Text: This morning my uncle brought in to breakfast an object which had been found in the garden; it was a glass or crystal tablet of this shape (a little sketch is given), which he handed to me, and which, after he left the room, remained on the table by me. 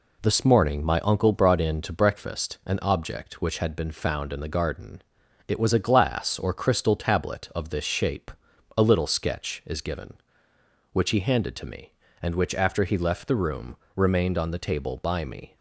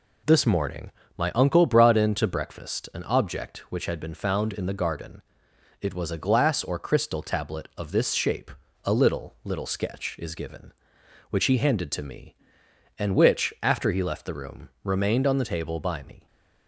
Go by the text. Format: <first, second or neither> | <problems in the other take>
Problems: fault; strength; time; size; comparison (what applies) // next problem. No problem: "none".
first | pauses between "morning" and "my"; slight; at 0.9 s; 0.28 s long // says "little" twice; at 9.4 s